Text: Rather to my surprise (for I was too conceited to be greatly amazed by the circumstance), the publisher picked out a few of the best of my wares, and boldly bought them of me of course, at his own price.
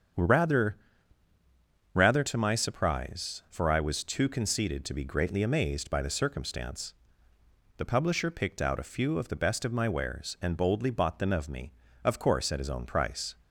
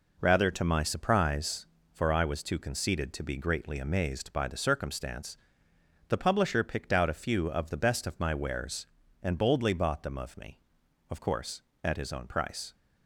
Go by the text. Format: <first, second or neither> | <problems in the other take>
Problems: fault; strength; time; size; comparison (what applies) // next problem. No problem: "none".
second | starts louder than the rest; strong; until 2.3 s; 7.5 dB // says "Rather" twice; at 1.9 s